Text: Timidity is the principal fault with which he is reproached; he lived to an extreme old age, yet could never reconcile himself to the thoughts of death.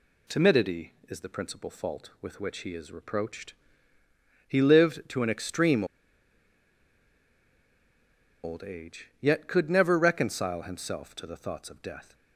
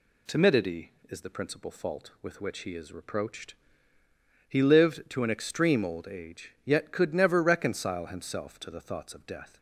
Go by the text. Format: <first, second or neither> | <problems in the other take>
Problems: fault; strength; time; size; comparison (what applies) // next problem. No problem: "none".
second | pauses between "extreme" and "old"; strong; at 5.8 s; 2.5 s long